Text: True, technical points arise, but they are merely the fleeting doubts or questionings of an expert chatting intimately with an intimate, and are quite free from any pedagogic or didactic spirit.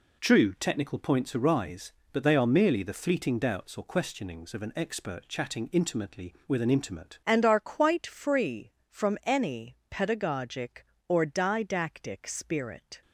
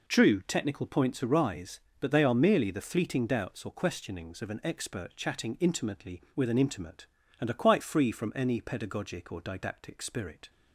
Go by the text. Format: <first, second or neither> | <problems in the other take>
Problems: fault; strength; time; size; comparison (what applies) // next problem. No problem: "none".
second | changes voice at "and"; from 7.2 s on; 5.8 s long